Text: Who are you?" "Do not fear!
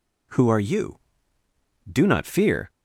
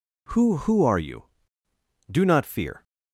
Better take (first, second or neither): first